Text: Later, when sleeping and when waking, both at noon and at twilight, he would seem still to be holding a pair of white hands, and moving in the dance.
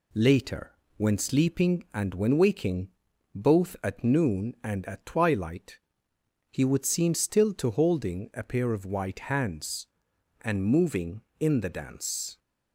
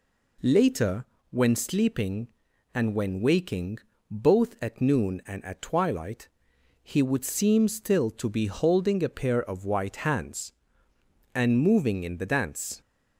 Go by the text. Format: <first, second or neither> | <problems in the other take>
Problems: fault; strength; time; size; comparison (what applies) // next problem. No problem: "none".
second | skips "be"; at 7.7 s